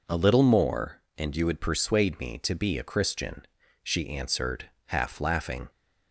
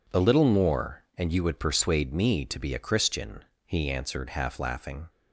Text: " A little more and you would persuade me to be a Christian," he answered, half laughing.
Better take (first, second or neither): second